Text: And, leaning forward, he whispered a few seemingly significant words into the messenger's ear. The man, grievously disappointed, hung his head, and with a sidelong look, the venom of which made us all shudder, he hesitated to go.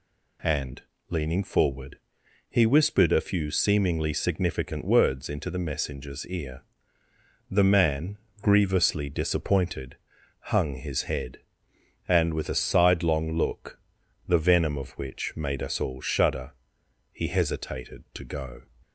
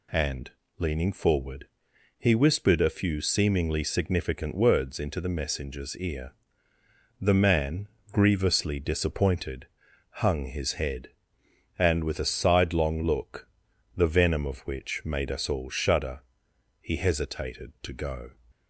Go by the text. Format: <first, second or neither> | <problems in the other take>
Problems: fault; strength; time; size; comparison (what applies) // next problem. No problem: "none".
neither | none